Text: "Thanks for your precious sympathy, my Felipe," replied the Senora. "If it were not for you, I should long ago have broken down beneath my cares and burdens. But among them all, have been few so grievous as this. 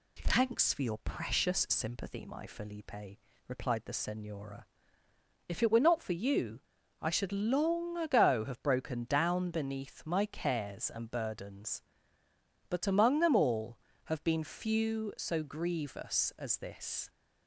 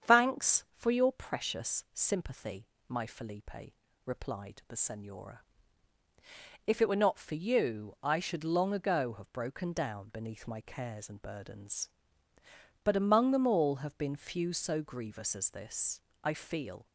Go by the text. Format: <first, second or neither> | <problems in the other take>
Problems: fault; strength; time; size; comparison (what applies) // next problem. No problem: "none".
first | starts louder than the rest; strong; until 1.1 s; 8 dB // goes on to say "I feel"; noticeable; from 16.2 s on; 0.64 s long